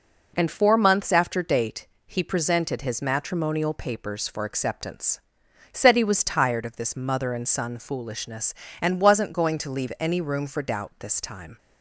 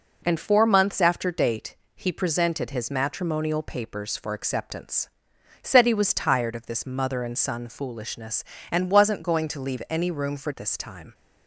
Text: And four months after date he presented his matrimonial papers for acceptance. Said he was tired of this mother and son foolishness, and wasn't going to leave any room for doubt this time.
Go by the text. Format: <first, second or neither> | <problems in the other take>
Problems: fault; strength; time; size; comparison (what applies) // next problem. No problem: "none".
first | pauses between "date" and "he"; slight; at 1.7 s; 0.20 s long; slight in the first // skips "doubt"; at 10.5 s